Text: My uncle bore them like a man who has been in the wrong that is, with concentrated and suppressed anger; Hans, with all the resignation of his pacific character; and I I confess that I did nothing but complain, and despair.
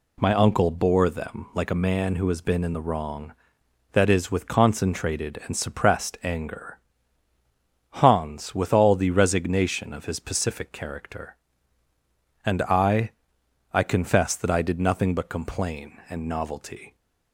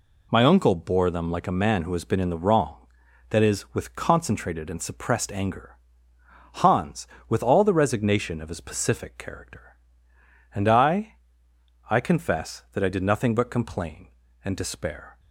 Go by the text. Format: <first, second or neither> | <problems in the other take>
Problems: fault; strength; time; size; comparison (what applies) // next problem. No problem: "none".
second | pauses between "I" and "I"; noticeable; at 13.1 s; 0.64 s long; noticeable in the second // says "novelty" for "despair"; at 16.2 s